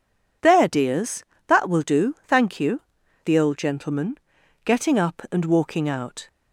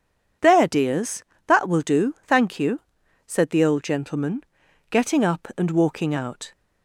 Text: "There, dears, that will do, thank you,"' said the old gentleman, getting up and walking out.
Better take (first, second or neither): second